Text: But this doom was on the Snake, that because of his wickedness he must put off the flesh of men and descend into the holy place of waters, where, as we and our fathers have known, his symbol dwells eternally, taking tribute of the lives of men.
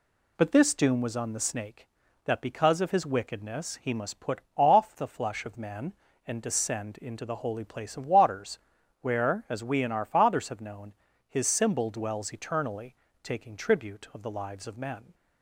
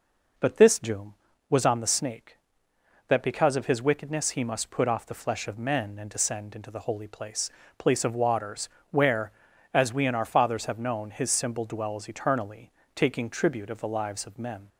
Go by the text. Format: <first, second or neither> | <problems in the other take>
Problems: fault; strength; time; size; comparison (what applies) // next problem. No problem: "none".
first | says "place" twice; at 7.7 s